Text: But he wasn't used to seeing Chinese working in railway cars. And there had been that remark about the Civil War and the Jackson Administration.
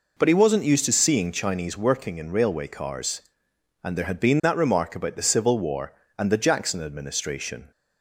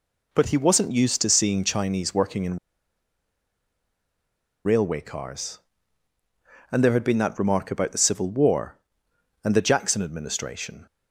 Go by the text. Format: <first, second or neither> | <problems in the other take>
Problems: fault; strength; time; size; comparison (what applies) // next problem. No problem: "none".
first | pauses between "in" and "railway"; strong; at 2.5 s; 2.0 s long